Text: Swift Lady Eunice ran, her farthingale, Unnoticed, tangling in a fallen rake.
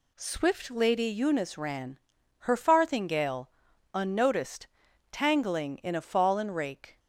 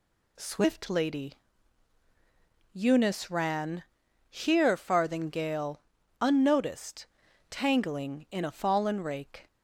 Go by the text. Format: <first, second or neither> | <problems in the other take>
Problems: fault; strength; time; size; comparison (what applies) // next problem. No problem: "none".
first | pauses between "Lady" and "Eunice"; strong; at 1.3 s; 1.4 s long // says "here" for "her"; at 4.2 s